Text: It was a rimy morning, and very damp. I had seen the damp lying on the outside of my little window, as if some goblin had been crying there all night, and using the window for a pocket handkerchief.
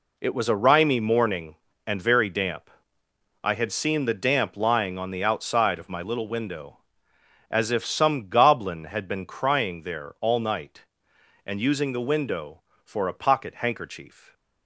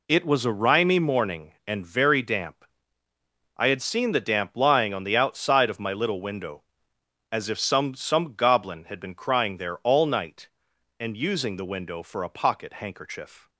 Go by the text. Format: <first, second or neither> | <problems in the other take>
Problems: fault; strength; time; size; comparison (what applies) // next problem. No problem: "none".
first | says "some" twice; at 7.9 s